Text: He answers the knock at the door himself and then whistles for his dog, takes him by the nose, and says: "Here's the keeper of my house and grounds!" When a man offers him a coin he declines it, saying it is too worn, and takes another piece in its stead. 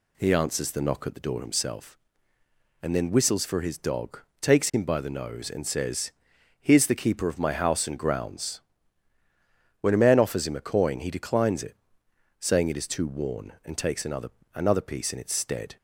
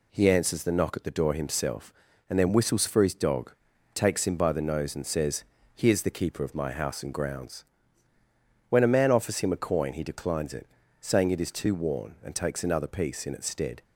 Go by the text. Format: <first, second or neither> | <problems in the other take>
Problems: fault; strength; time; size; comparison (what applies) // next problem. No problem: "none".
second | says "another" twice; at 14.5 s